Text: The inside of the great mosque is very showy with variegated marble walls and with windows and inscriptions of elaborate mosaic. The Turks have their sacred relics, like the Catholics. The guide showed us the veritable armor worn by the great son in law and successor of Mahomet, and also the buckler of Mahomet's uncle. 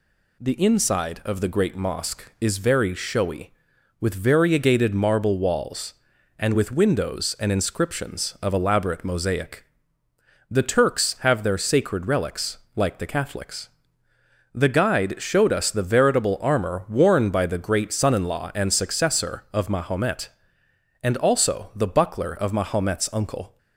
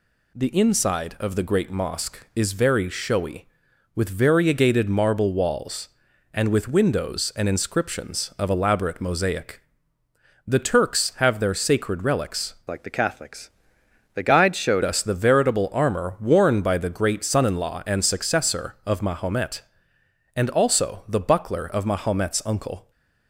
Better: first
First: none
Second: changes voice from "like" to "showed"; from 12.6 to 14.8 s; 2.2 s long

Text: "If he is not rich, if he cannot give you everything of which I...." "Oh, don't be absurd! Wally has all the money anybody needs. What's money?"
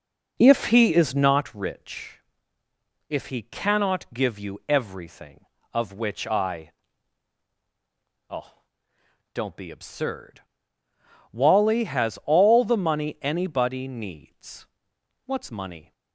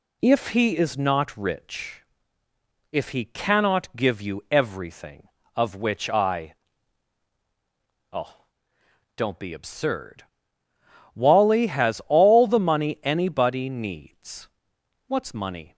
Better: second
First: starts louder than the rest; noticeable; until 1.5 s; 4.5 dB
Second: none

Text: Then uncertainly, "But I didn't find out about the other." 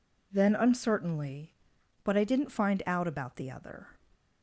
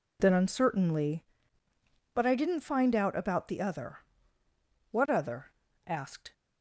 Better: first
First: none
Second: goes on to say "What other asked"; from 4.9 s on; 1.4 s long

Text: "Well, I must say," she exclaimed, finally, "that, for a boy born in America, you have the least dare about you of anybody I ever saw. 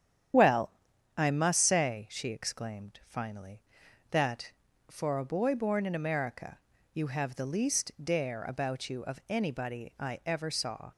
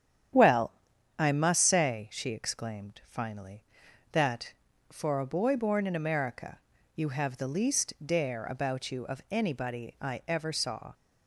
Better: second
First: loses the start of "Well"; at 0.3 s; 25 ms // starts louder than the rest; strong; until 1.7 s; 9.5 dB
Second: starts louder than the rest; strong; until 1.7 s; 9.5 dB

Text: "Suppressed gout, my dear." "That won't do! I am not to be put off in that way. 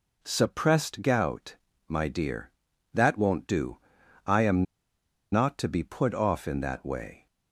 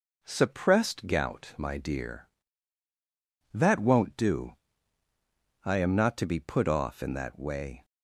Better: second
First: pauses between "am" and "not"; noticeable; at 4.6 s; 0.68 s long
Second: none

